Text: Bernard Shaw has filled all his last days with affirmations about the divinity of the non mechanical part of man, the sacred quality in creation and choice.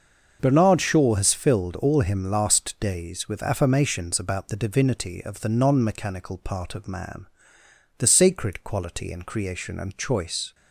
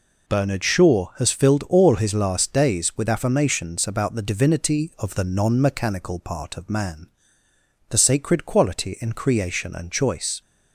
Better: second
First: starts louder than the rest; until 1.4 s; 6.5 dB // says "him" for "his"; at 2.0 s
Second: none

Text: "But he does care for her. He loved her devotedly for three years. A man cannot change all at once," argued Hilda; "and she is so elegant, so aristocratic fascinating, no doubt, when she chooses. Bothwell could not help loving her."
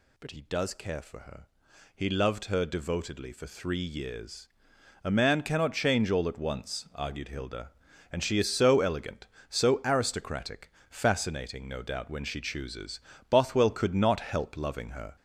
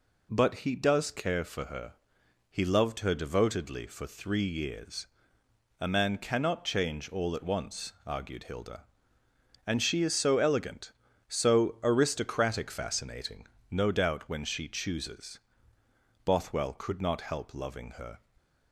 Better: second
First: gets louder; noticeable; throughout; 4 dB // pauses between "aristocratic" and "fascinating"; slight; at 10.7 s; 0.18 s long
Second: none

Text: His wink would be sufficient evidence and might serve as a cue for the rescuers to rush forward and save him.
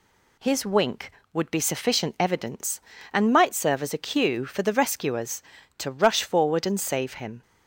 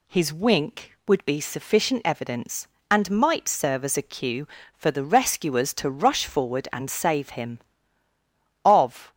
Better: first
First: none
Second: goes on to say "Of"; slight; from 8.6 s on; 0.48 s long

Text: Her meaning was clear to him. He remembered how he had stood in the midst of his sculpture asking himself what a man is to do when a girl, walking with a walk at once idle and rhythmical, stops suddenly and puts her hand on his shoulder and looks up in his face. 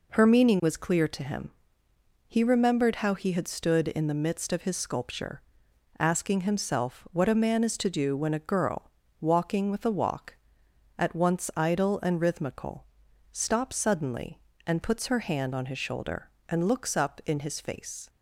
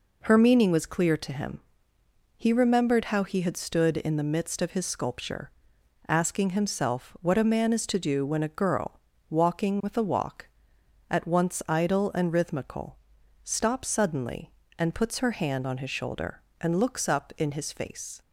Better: neither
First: pauses between "sculpture" and "asking"; noticeable; at 5.4 s; 0.58 s long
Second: pauses between "sculpture" and "asking"; noticeable; at 5.4 s; 0.58 s long

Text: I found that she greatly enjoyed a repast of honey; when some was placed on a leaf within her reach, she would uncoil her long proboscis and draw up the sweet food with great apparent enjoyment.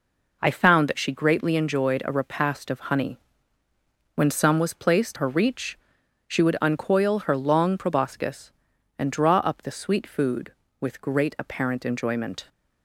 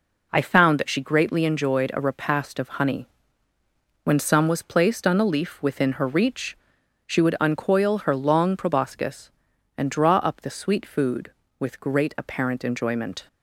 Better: second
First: skips "on a leaf within"; at 5.1 s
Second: none

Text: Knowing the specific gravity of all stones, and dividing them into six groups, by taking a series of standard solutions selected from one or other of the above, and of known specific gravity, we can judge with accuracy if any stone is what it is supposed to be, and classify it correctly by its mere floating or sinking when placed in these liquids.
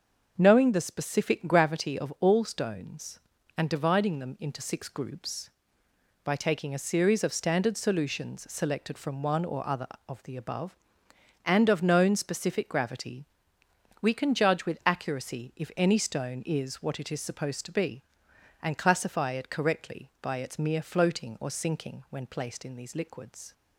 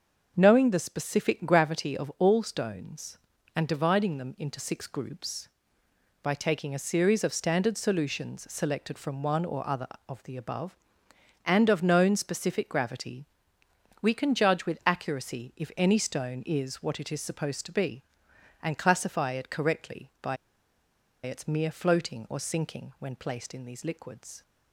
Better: first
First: starts louder than the rest; until 1.4 s; 6.5 dB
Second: starts louder than the rest; until 1.3 s; 6.5 dB // pauses between "by" and "its"; noticeable; at 20.3 s; 0.89 s long

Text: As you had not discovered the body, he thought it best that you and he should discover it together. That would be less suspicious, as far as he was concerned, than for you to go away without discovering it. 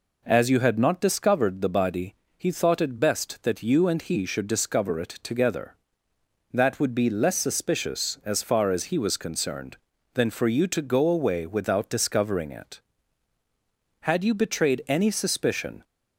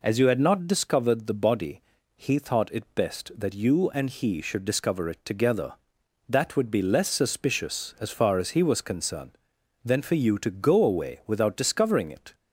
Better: second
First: goes on to say "Had you betrayed any suspicion"; strong; from 14.0 s on; 1.8 s long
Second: none

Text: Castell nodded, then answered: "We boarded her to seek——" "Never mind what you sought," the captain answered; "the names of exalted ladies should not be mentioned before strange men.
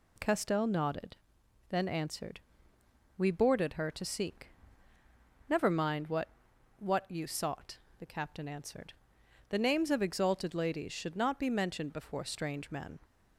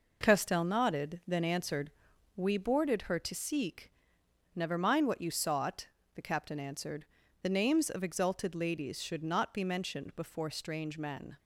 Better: second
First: says "what" twice; at 6.7 s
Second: none

